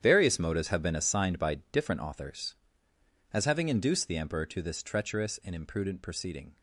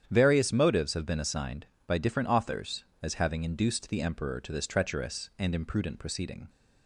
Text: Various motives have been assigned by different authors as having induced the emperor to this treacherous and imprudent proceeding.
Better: second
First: gets quieter; strong; throughout; 14 dB // starts louder than the rest; strong; until 1.0 s; 10 dB // pauses between "by" and "different"; slight; at 1.5 s; 0.16 s long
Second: starts louder than the rest; strong; until 1.1 s; 9 dB

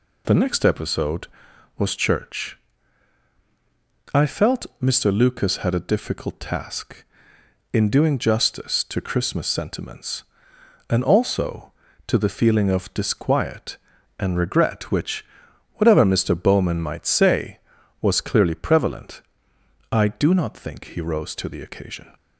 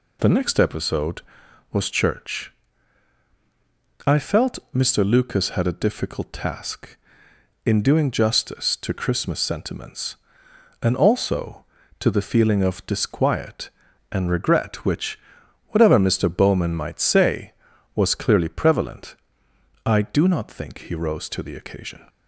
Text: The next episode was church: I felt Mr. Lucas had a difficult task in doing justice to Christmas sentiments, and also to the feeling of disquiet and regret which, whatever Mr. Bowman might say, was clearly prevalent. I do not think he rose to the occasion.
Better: neither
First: none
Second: none

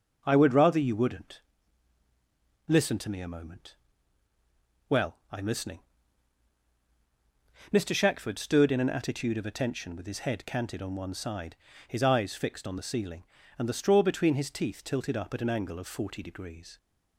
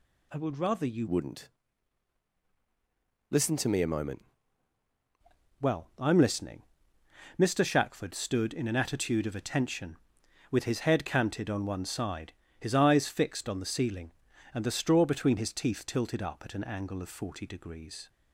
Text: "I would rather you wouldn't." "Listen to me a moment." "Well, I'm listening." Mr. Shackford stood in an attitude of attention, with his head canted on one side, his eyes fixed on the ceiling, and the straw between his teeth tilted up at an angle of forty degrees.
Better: first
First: none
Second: changes voice from "wouldn't" to "moment"; from 1.0 to 4.2 s; 3.2 s long

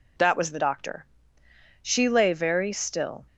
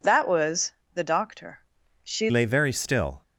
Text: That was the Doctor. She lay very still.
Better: first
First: none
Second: pauses between "was" and "the"; slight; at 0.7 s; 0.22 s long // changes voice at "lay"; from 2.2 s on; 1.0 s long

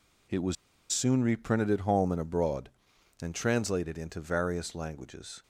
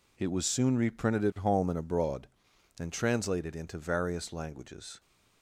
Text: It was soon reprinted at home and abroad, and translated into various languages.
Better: second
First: pauses between "was" and "soon"; at 0.5 s; 0.37 s long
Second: none

